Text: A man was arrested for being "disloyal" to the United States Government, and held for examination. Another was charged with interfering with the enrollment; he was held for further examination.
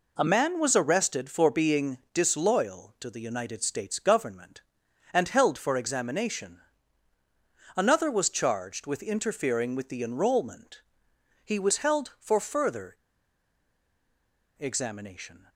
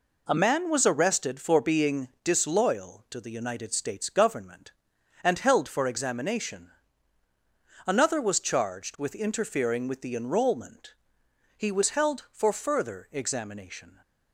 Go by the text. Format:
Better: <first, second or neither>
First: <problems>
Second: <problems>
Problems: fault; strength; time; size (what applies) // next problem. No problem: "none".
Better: second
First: pauses between "being" and "disloyal"; slight; at 1.9 s; 0.16 s long // pauses between "further" and "examination"; strong; at 12.9 s; 1.6 s long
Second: pauses between "being" and "disloyal"; slight; at 2.0 s; 0.16 s long